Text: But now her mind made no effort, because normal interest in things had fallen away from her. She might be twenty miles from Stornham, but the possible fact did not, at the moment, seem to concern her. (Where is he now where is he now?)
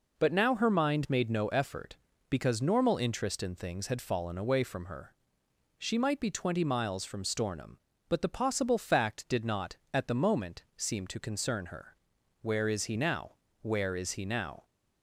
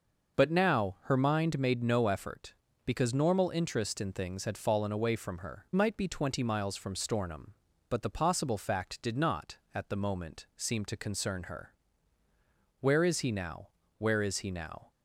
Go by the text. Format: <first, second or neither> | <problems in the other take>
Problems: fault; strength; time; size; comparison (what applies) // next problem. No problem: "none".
first | starts louder than the rest; noticeable; until 1.4 s; 6 dB // skips "She"; at 5.6 s // pauses between "now" and "where"; slight; at 13.6 s; 0.30 s long; slight in the first